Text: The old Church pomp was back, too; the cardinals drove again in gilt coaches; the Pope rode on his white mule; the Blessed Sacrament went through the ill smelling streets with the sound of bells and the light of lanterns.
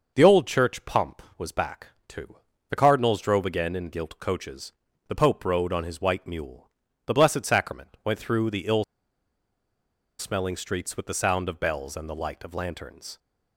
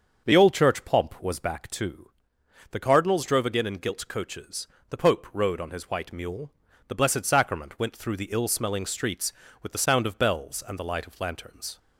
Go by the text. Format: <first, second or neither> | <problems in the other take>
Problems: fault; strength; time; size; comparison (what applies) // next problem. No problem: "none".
second | starts louder than the rest; noticeable; until 1.1 s; 6 dB; also in the second // pauses between "ill" and "smelling"; strong; at 8.8 s; 1.3 s long